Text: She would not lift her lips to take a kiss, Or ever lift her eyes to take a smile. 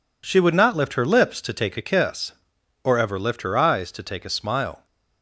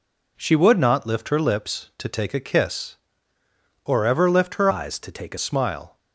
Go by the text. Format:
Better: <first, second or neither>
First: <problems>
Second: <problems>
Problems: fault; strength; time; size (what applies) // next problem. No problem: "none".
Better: first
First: none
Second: changes voice from "eyes" to "a"; from 4.6 to 5.3 s; 0.7 s long